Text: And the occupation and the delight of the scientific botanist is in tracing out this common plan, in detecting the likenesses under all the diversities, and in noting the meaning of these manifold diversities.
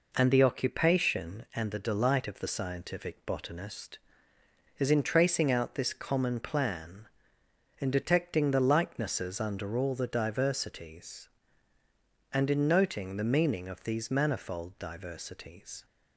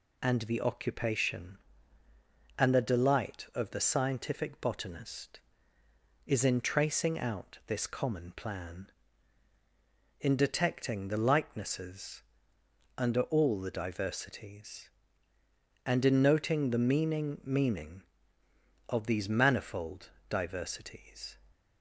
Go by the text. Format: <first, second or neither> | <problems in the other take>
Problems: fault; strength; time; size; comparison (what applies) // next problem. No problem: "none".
first | pauses between "likenesses" and "under"; noticeable; at 12.2 s; 0.74 s long // says "meaning" twice; at 17.4 s // pauses between "manifold" and "diversities"; slight; at 20.1 s; 0.18 s long